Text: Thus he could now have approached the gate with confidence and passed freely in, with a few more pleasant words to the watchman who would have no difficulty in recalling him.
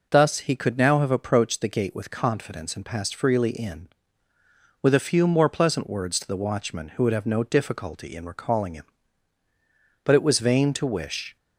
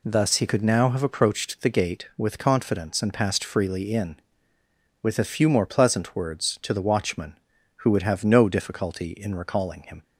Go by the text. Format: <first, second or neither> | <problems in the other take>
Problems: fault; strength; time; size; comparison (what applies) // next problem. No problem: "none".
second | goes on to say "But it was vain to wish"; from 10.0 s on; 1.3 s long